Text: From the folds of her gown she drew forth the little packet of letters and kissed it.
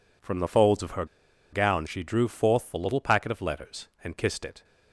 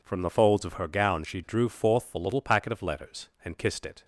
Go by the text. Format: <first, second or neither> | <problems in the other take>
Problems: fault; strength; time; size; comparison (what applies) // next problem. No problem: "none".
second | pauses between "her" and "gown"; noticeable; at 1.0 s; 0.47 s long